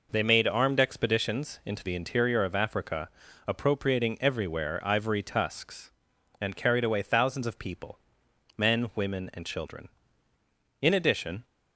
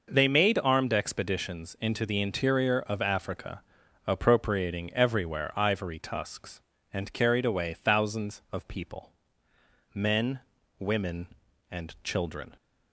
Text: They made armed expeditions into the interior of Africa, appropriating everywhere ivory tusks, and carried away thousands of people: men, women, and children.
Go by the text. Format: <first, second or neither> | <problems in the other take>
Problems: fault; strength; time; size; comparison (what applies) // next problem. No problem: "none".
second | goes on to say "In addition"; noticeable; from 10.8 s on; 0.62 s long